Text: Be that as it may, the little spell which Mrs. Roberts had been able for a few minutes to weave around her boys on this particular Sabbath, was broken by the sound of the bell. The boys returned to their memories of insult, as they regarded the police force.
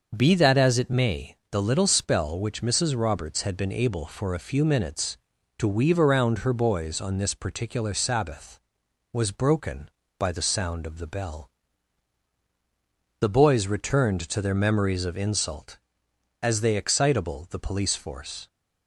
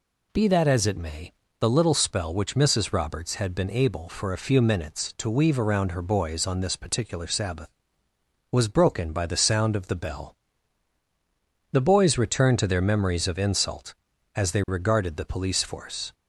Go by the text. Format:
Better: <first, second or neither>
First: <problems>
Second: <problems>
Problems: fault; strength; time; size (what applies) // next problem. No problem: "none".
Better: second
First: starts louder than the rest; noticeable; until 1.1 s; 6 dB // says "excitable" for "regarded"; at 16.7 s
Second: none